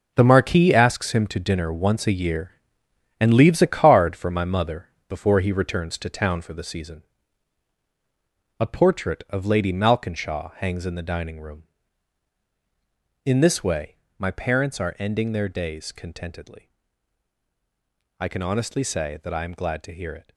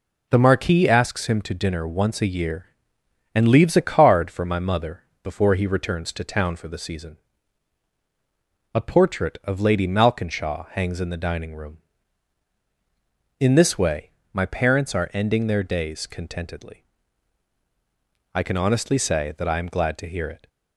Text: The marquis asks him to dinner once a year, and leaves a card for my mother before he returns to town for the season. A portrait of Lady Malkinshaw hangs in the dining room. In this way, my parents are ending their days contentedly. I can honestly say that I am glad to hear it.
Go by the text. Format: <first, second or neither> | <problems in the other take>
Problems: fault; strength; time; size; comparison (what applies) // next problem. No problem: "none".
second | gets quieter; strong; throughout; 10.5 dB // pauses between "mother" and "before"; slight; at 4.8 s; 0.18 s long; slight in the second